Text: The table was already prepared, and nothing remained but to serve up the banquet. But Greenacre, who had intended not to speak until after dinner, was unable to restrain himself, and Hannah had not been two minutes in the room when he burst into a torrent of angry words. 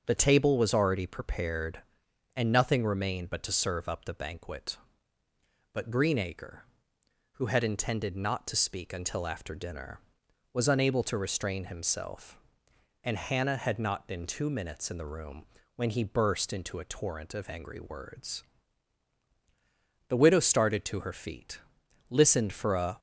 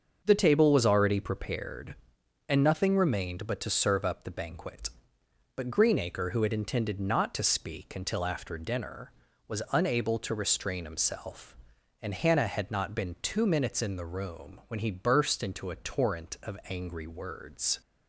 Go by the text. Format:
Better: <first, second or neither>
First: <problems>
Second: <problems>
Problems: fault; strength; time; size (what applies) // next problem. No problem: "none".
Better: second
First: starts louder than the rest; until 1.0 s; 6.5 dB // pauses between "room" and "when"; slight; at 15.4 s; 0.28 s long // goes on to say "The widow started to her feet listened for a"; strong; from 20.0 s on; 2.9 s long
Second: starts louder than the rest; until 1.2 s; 6.5 dB